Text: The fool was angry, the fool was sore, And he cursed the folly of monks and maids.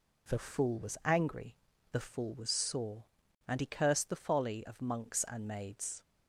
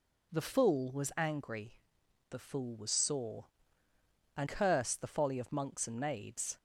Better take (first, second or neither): first